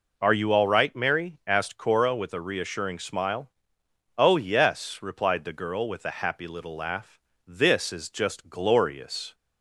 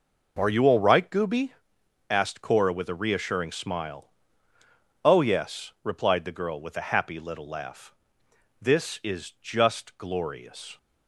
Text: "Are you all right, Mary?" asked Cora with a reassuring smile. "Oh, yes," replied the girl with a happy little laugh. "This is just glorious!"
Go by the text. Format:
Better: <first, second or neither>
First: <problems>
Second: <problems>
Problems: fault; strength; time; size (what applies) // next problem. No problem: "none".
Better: first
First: none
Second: says "Gooby" for "Mary"; at 1.0 s